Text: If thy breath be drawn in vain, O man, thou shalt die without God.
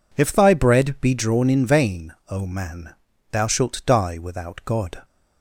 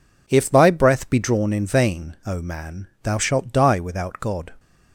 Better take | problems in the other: second | says "bread" for "breath"; at 0.5 s

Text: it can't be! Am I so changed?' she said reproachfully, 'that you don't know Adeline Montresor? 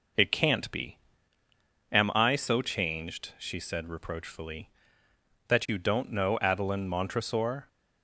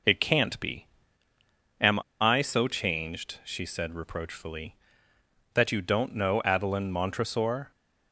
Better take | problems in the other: first | pauses between "Am" and "I"; slight; at 1.9 s; 0.21 s long

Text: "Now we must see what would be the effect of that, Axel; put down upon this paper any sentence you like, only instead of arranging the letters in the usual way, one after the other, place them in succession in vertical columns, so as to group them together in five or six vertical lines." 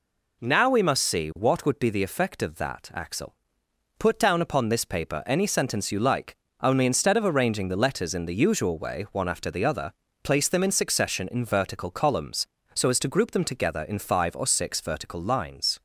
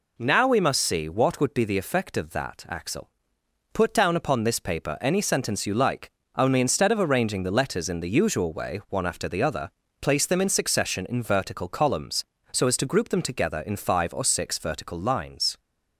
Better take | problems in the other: neither | none

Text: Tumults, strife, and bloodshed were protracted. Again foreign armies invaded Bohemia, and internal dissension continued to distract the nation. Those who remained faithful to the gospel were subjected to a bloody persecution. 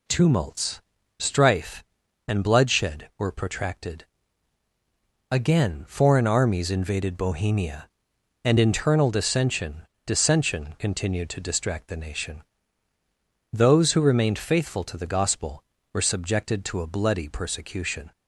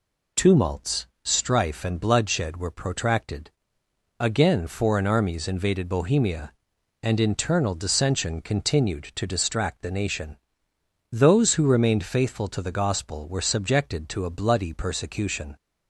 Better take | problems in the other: second | says "dissension" twice; at 10.0 s

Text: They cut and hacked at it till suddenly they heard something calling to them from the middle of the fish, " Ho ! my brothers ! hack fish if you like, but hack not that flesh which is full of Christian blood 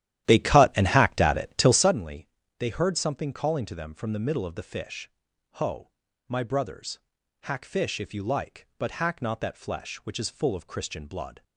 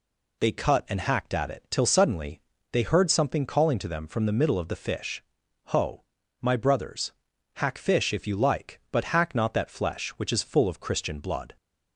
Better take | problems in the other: second | starts louder than the rest; strong; until 2.0 s; 12.5 dB // pauses between "suddenly" and "they"; slight; at 2.2 s; 0.32 s long; slight in the second

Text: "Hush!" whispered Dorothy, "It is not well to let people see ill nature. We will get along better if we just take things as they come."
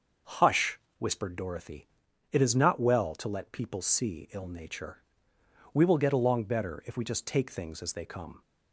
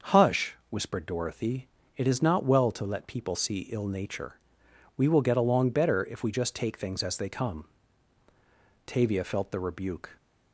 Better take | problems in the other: first | starts louder than the rest; until 1.2 s; 6.5 dB; also in the first // goes on to say "Tavia felt the rebuke"; noticeable; from 8.8 s on; 1.3 s long

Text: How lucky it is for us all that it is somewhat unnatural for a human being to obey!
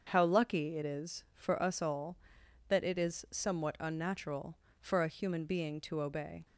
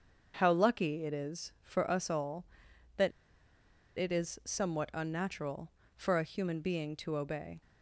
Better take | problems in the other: first | starts louder than the rest; until 1.3 s; 6.5 dB; also in the first // pauses between "that" and "it"; noticeable; at 3.1 s; 0.87 s long

